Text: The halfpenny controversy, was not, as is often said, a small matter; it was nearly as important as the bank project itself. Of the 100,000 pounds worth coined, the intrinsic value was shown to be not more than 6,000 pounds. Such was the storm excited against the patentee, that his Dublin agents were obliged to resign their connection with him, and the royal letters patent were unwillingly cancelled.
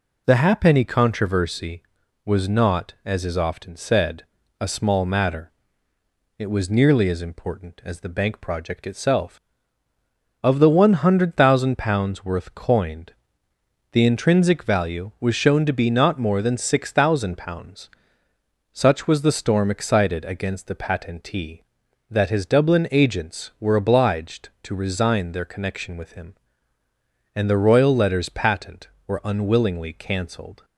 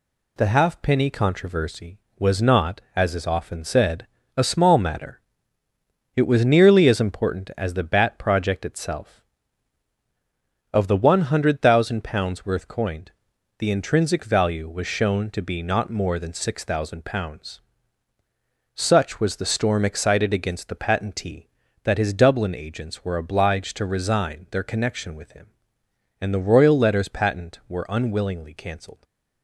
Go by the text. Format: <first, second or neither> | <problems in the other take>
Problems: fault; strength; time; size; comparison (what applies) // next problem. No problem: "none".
first | says "bat" for "bank"; at 7.8 s